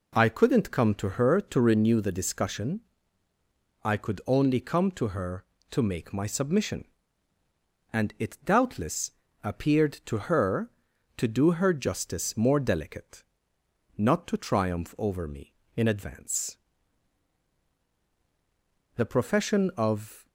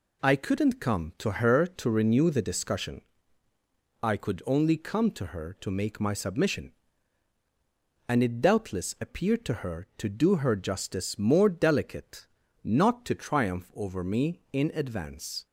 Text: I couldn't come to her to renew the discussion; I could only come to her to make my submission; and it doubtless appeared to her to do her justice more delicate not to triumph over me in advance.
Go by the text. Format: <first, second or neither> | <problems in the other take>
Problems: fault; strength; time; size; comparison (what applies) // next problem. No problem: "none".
second | pauses between "doubtless" and "appeared"; slight; at 9.0 s; 0.32 s long // pauses between "delicate" and "not"; noticeable; at 13.2 s; 0.72 s long; also in the second // goes on to say "The profession of"; from 18.9 s on; 1.3 s long